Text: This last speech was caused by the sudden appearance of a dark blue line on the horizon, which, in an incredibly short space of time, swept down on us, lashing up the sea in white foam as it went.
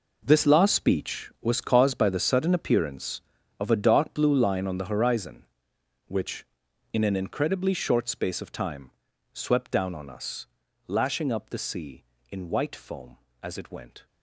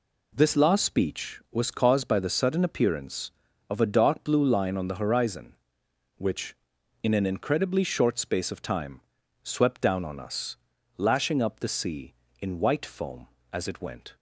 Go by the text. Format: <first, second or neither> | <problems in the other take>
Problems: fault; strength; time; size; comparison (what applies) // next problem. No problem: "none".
second | gets quieter; strong; throughout; 13 dB